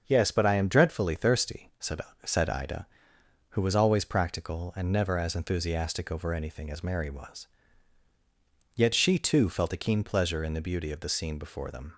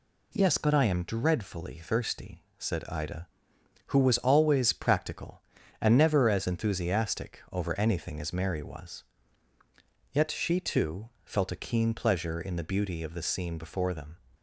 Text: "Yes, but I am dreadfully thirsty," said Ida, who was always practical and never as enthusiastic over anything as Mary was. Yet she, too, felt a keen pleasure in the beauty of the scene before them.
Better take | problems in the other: second | starts louder than the rest; until 1.0 s; 6.5 dB // says "said" twice; at 2.2 s

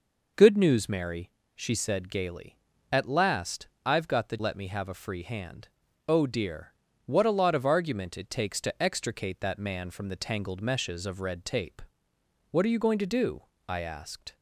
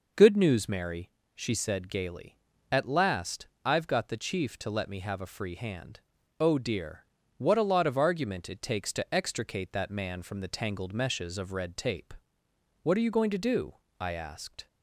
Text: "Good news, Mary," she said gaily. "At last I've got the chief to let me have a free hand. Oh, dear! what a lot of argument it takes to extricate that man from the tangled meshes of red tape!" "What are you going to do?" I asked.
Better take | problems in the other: second | pauses between "last" and "I've"; slight; at 3.6 s; 0.18 s long; slight in the second // skips "chief to"; at 4.3 s

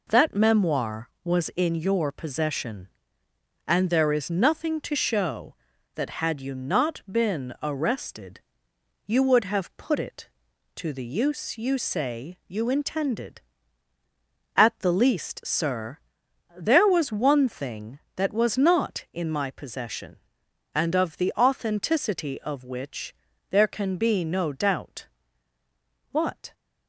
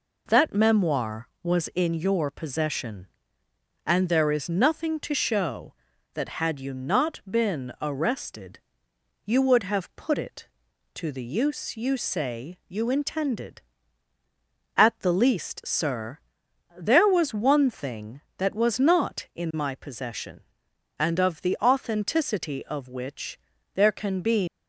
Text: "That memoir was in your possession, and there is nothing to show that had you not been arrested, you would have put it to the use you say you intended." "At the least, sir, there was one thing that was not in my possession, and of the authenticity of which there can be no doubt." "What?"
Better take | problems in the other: first | pauses between "which" and "there"; slight; at 23.3 s; 0.34 s long; slight in the first // stops before "no doubt What"; at 24.4 s

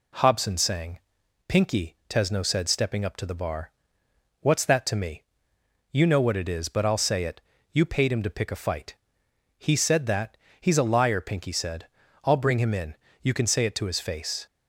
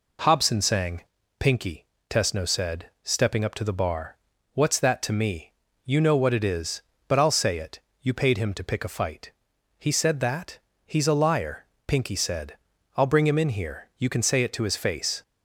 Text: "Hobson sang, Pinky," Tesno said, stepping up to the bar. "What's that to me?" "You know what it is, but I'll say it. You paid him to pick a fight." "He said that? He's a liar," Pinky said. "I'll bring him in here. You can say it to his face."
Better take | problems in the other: second | skips "here"; at 13.0 s

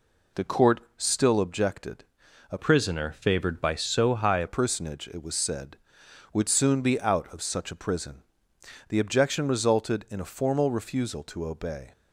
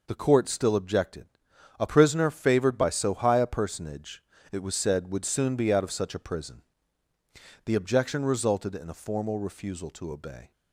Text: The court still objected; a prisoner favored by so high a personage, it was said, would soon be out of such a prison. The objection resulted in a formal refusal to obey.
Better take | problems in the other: second | pauses between "court" and "still"; slight; at 0.7 s; 0.18 s long // changes voice from "prisoner" to "a"; from 2.5 to 4.4 s; 1.9 s long

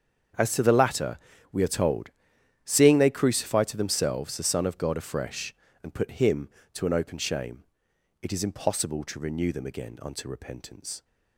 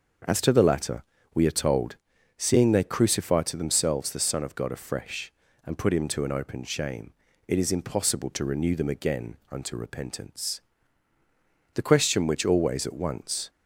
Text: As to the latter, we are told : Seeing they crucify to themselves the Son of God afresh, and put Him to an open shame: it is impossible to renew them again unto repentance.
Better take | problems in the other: first | starts louder than the rest; until 1.5 s; 6 dB; strong in the first // pauses between "again" and "unto"; slight; at 9.3 s; 0.16 s long // goes on to say "The question which always at once"; strong; from 11.7 s on; 1.7 s long

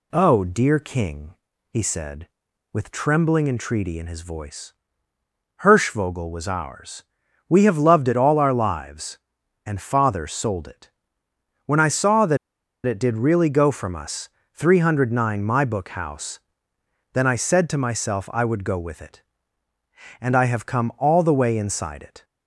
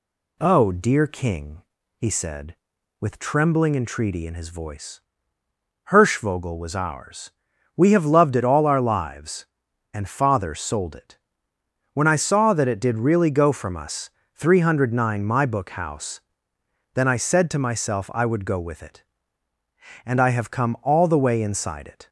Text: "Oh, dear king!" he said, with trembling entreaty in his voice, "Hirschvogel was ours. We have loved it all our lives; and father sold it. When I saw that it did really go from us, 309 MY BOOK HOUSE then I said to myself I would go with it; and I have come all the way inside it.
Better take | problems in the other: second | pauses between "that" and "it"; noticeable; at 12.3 s; 0.48 s long // pauses between "HOUSE" and "then"; noticeable; at 16.3 s; 0.72 s long; noticeable in the second

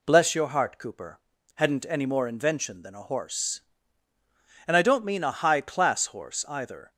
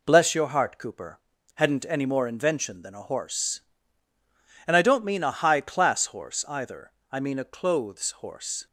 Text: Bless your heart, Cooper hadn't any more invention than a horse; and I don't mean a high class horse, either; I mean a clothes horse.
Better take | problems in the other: second | pauses between "Cooper" and "hadn't"; at 1.1 s; 0.38 s long; also in the second // stops before "I mean a clothes horse"; at 6.9 s

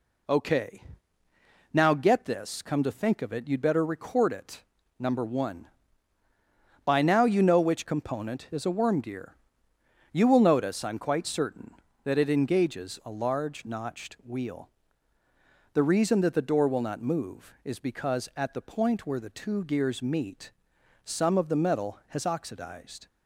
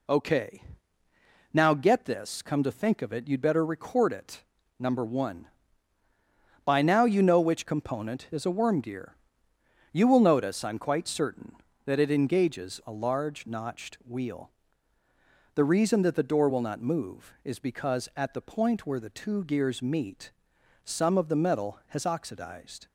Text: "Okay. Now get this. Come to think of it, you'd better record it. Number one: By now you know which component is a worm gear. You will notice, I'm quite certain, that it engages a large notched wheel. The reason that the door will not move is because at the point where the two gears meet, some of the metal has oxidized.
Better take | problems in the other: neither | none

